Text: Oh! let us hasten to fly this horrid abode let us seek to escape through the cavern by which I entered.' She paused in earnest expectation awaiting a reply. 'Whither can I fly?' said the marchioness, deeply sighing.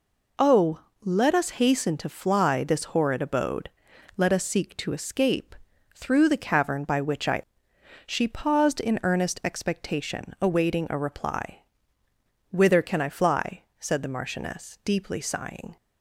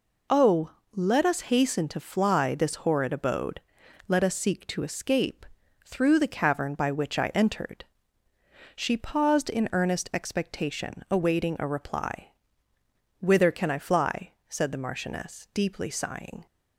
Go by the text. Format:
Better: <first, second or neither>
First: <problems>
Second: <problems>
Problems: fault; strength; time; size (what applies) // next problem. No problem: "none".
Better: second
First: pauses between "abode" and "let"; noticeable; at 3.6 s; 0.46 s long // pauses between "escape" and "through"; at 5.5 s; 0.44 s long // skips "entered"; at 7.7 s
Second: pauses between "abode" and "let"; noticeable; at 3.6 s; 0.46 s long // pauses between "escape" and "through"; at 5.4 s; 0.44 s long